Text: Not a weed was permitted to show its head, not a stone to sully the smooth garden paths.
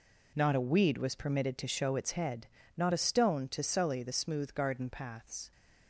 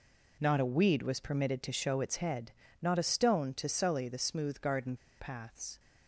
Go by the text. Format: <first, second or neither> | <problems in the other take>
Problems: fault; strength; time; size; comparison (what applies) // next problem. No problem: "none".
first | pauses between "garden" and "paths"; slight; at 4.9 s; 0.23 s long